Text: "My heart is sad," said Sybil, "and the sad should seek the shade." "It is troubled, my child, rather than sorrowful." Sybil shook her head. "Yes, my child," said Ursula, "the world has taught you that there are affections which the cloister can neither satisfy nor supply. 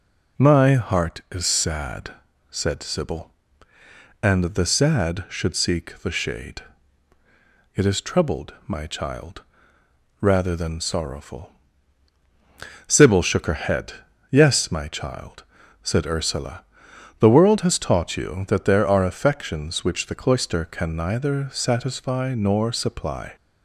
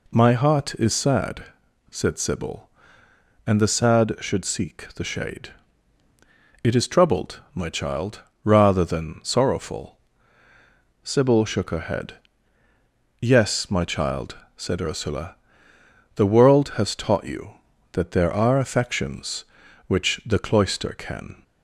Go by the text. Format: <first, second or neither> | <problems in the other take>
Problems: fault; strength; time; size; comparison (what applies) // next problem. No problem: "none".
first | stops before "neither satisfy nor supply"; at 21.4 s